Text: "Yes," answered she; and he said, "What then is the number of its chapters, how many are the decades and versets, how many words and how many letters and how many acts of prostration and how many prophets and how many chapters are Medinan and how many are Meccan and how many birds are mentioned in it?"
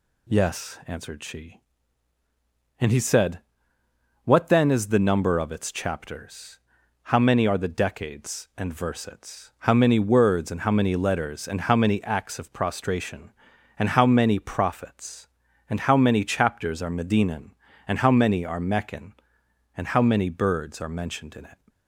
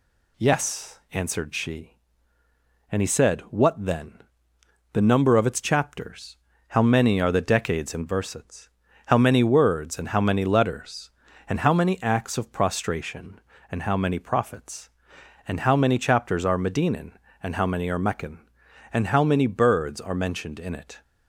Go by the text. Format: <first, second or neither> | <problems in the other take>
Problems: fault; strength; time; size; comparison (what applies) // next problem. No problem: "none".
first | skips "is"; at 4.5 s